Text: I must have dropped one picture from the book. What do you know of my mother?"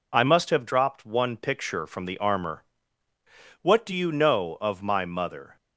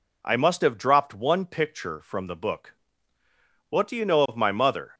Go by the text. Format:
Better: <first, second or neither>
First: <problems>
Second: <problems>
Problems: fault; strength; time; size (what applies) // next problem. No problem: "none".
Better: second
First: says "armor" for "book"; at 2.1 s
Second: none